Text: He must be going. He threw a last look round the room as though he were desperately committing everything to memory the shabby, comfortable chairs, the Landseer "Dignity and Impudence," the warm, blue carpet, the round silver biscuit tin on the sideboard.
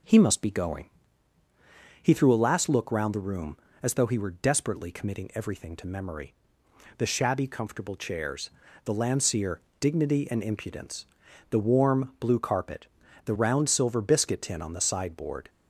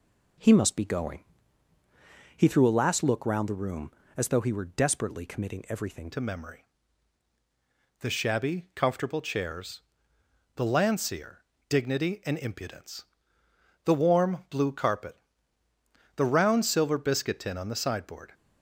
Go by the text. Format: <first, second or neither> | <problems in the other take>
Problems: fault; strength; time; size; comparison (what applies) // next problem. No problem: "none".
first | changes voice at "to"; from 6.1 s on; 12.2 s long // pauses between "memory" and "the"; strong; at 6.5 s; 1.4 s long; noticeable in the first // pauses between "Landseer" and "Dignity"; slight; at 11.4 s; 0.24 s long; slight in the first